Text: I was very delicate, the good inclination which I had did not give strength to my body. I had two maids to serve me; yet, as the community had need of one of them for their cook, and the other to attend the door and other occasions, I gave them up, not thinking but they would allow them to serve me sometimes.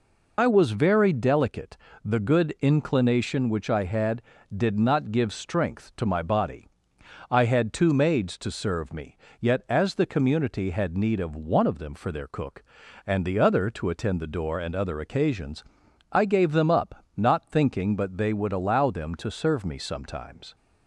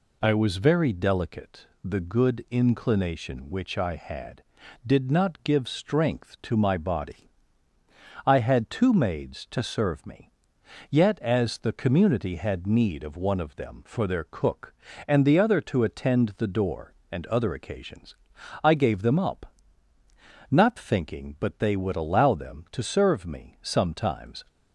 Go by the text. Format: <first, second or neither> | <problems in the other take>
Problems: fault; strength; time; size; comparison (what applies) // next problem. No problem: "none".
second | loses the start of "I"; at 0.3 s; 70 ms